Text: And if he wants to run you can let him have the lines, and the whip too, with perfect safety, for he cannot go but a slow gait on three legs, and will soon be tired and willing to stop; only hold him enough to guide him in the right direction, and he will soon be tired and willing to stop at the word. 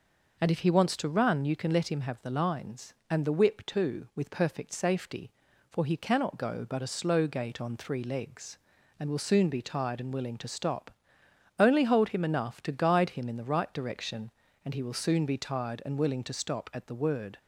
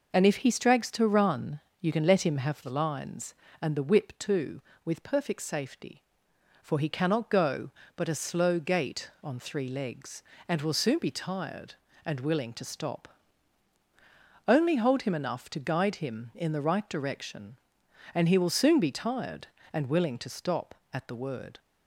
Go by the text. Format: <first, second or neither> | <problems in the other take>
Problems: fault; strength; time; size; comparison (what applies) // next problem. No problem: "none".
first | says "strags" for "wants"; at 0.5 s // pauses between "run" and "you"; slight; at 1.6 s; 0.20 s long